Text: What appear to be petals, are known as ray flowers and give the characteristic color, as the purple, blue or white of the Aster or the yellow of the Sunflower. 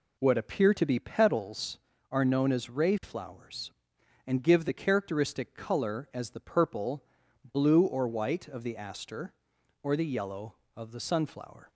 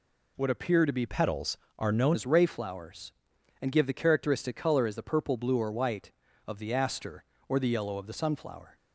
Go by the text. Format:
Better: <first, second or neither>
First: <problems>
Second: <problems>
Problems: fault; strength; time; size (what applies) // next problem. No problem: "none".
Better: first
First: none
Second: changes voice from "petals" to "known"; from 1.0 to 2.1 s; 1.1 s long